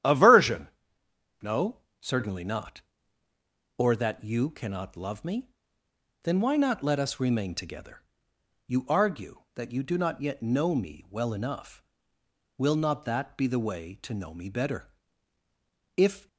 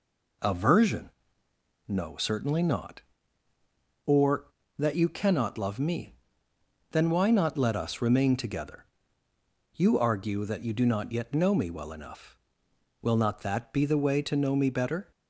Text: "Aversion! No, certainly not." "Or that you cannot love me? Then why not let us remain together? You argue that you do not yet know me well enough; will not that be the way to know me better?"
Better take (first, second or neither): second